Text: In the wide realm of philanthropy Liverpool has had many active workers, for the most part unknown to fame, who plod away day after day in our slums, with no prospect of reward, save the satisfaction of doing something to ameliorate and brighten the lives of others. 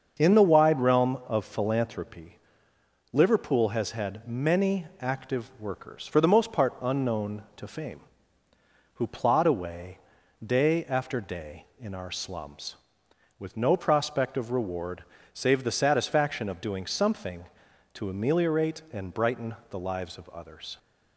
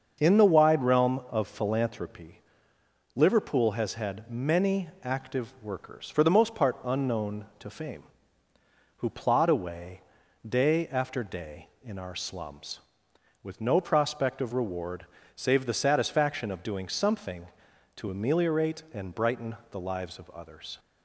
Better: neither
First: starts louder than the rest; until 1.1 s; 6.5 dB // pauses between "philanthropy" and "Liverpool"; noticeable; at 2.3 s; 0.74 s long // pauses between "away" and "day"; noticeable; at 9.9 s; 0.46 s long // pauses between "brighten" and "the"; slight; at 19.5 s; 0.16 s long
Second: starts louder than the rest; until 1.1 s; 6.5 dB // pauses between "philanthropy" and "Liverpool"; noticeable; at 2.4 s; 0.74 s long // pauses between "away" and "day"; noticeable; at 10.0 s; 0.46 s long // pauses between "brighten" and "the"; slight; at 19.5 s; 0.16 s long

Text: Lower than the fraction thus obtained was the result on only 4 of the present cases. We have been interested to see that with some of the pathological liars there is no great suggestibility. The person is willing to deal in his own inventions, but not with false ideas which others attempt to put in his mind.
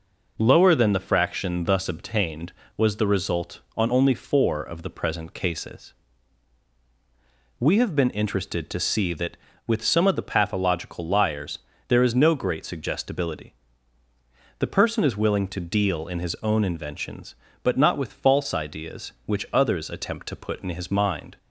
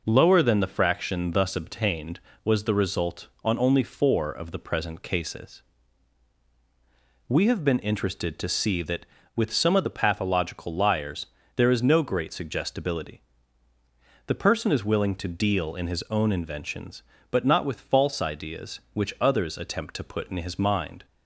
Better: neither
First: pauses between "liars" and "there"; slight; at 11.5 s; 0.28 s long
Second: pauses between "liars" and "there"; slight; at 11.2 s; 0.28 s long

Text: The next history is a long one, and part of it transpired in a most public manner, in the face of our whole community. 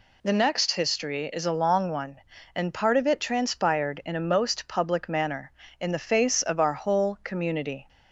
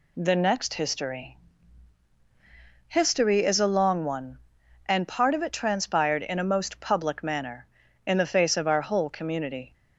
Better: first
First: none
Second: says "history" twice; at 2.8 s

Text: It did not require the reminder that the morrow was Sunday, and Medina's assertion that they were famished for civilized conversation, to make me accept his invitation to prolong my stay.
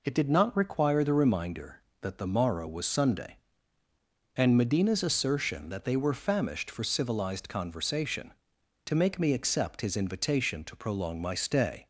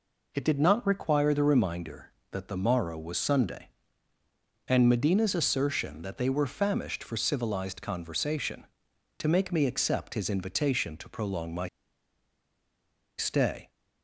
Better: first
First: none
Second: pauses between "my" and "stay"; strong; at 11.6 s; 1.5 s long

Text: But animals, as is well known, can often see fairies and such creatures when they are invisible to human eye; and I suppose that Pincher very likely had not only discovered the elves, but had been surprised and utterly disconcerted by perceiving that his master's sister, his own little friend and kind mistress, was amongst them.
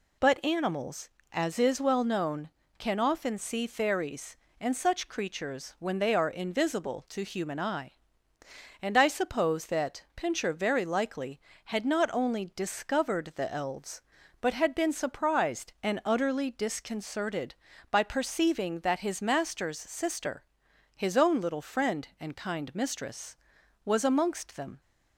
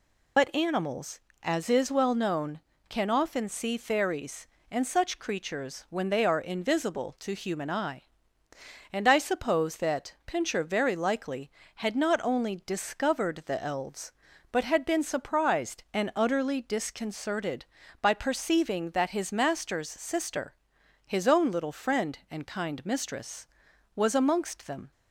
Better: first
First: none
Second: loses the start of "But"; at 0.3 s; 60 ms

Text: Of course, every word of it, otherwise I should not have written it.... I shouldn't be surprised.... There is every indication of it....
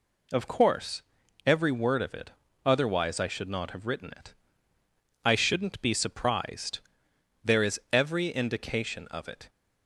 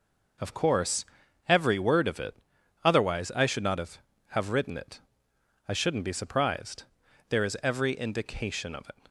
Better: first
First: none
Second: says "have" twice; at 4.2 s

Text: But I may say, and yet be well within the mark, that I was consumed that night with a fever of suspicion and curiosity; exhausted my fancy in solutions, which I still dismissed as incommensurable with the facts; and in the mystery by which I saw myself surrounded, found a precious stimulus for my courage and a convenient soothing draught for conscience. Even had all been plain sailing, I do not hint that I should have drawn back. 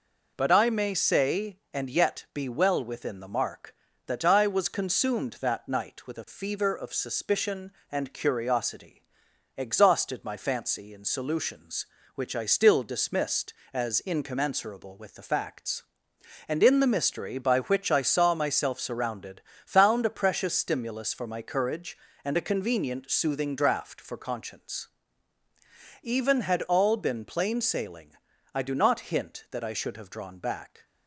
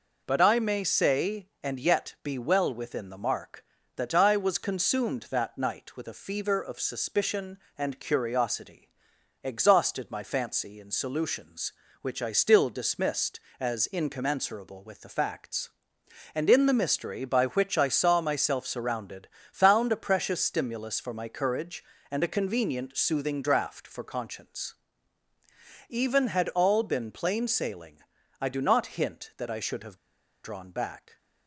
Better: first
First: none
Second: pauses between "have" and "drawn"; noticeable; at 29.9 s; 0.48 s long

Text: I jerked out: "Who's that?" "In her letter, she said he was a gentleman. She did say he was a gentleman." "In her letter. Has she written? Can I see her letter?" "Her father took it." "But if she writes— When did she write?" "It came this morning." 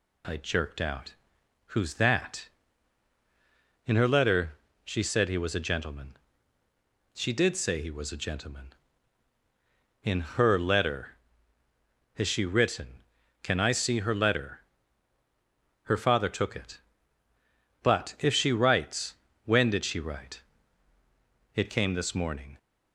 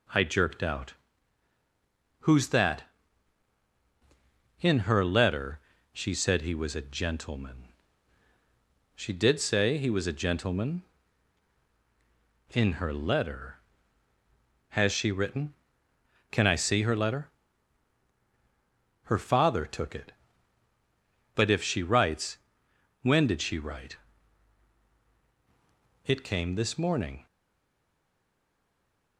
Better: first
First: none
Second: stays silent after the last word; noticeable; from 27.2 s on; 1.9 s long

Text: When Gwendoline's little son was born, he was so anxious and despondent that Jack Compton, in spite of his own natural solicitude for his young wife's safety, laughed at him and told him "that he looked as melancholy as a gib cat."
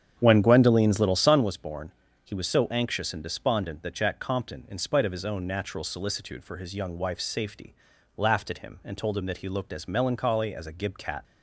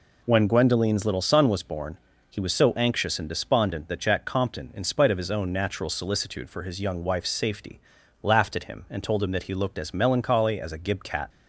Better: second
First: starts louder than the rest; strong; until 1.4 s; 8.5 dB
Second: none

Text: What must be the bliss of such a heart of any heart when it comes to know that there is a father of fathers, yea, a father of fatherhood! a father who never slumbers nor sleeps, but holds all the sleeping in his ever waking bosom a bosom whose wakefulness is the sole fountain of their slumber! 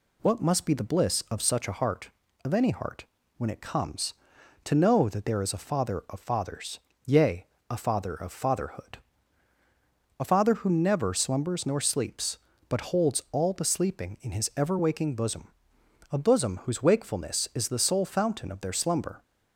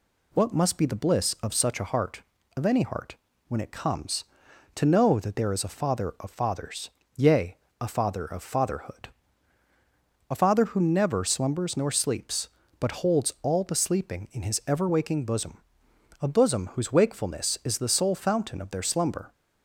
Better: neither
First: pauses between "heart" and "when"; slight; at 3.0 s; 0.32 s long // pauses between "bosom" and "a"; noticeable; at 15.4 s; 0.64 s long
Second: pauses between "heart" and "when"; slight; at 3.1 s; 0.32 s long // pauses between "bosom" and "a"; noticeable; at 15.5 s; 0.64 s long

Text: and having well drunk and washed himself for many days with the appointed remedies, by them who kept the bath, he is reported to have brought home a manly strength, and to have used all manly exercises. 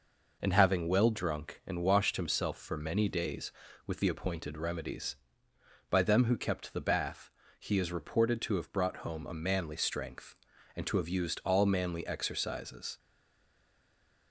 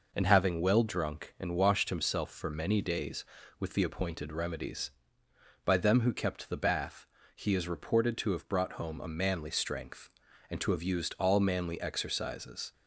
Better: second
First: stays silent after the last word; noticeable; from 12.9 s on; 1.4 s long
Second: none

